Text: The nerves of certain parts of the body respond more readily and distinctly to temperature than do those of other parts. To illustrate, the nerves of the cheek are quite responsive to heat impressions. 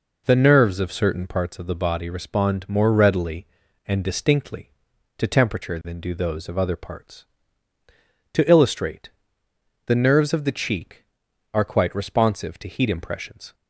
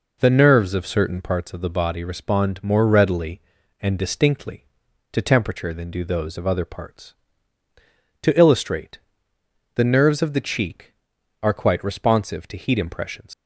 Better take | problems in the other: first | leaves "impressions" unfinished; at 13.3 s; 90 ms

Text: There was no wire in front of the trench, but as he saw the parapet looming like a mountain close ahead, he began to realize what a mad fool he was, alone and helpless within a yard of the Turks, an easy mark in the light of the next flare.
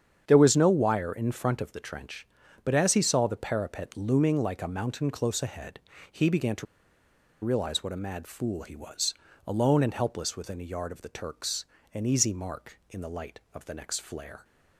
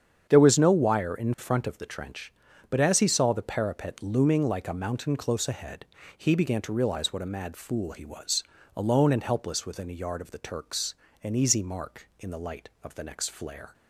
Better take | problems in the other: second | starts louder than the rest; strong; until 1.2 s; 8 dB; strong in the second // pauses between "to" and "realize"; noticeable; at 6.6 s; 0.78 s long

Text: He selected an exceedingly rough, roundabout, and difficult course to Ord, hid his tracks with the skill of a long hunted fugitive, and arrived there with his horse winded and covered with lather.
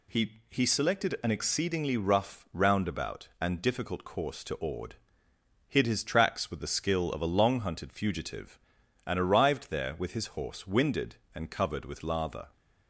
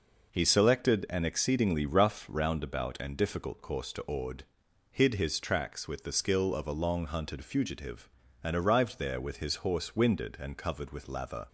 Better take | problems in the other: second | says "He" twice; at 0.4 s

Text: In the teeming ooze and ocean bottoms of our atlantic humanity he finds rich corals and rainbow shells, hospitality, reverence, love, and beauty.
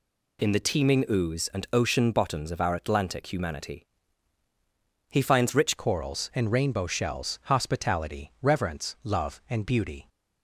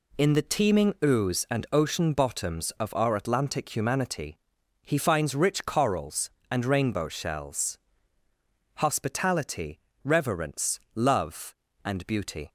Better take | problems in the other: second | pauses between "humanity" and "he"; at 3.8 s; 1.2 s long; noticeable in the second // changes voice at "corals"; from 5.7 s on; 4.3 s long

